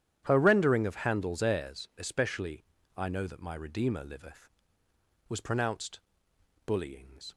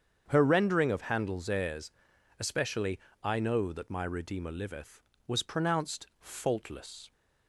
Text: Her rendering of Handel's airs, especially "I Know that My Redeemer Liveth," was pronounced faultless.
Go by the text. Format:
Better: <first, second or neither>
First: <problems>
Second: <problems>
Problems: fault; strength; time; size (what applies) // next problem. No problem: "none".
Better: second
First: starts louder than the rest; strong; until 1.2 s; 10 dB // pauses between "especially" and "I"; slight; at 2.6 s; 0.32 s long // says "bullyings" for "faultless"; at 6.6 s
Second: starts louder than the rest; strong; until 1.2 s; 7.5 dB // pauses between "especially" and "I"; slight; at 2.9 s; 0.24 s long